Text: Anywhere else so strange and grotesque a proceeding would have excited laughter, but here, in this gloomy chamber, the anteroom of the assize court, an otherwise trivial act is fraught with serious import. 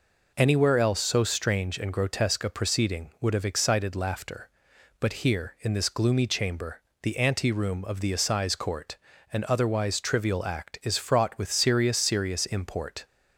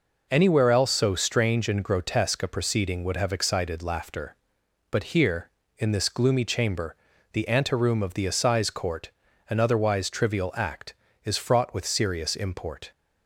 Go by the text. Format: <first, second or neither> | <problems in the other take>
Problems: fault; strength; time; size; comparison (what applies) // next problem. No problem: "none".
second | says "serious" twice; at 11.9 s